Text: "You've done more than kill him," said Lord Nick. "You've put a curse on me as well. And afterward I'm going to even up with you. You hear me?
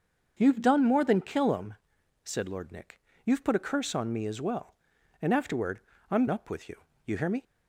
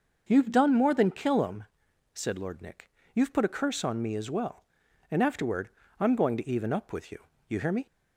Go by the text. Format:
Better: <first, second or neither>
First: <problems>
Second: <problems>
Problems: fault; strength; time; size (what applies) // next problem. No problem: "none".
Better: second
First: starts louder than the rest; until 1.3 s; 6.5 dB // pauses between "afterward" and "I'm"; slight; at 5.8 s; 0.30 s long // skips "going to even"; at 6.2 s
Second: pauses between "afterward" and "I'm"; slight; at 5.6 s; 0.30 s long